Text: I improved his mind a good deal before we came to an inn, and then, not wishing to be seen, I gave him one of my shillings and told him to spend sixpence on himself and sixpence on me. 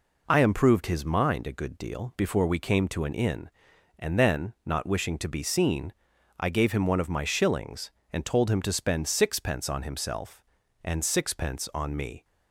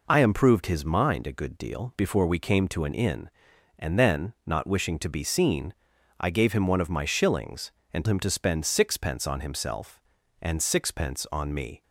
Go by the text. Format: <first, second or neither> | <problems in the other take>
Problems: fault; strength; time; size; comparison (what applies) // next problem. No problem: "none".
first | skips "told"; at 8.0 s